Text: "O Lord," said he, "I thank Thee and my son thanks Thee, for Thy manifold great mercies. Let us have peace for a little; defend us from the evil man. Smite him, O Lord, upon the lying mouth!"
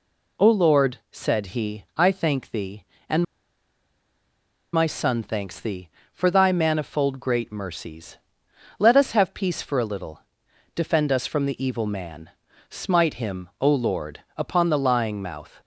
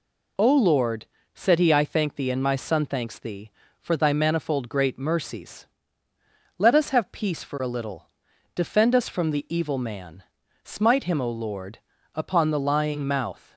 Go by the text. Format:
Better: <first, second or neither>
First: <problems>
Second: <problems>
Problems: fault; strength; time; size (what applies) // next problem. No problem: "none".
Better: second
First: pauses between "and" and "my"; strong; at 3.2 s; 1.4 s long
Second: none